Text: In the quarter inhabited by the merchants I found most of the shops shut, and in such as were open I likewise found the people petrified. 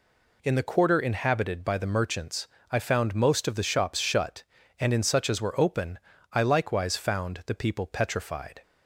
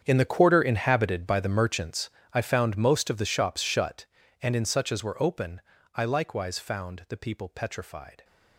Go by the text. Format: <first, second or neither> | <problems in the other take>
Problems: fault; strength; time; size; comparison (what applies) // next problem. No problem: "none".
first | gets quieter; strong; throughout; 16.5 dB // pauses between "merchants" and "I"; slight; at 2.1 s; 0.22 s long; slight in the first // pauses between "open" and "I"; slight; at 5.6 s; 0.34 s long; slight in the first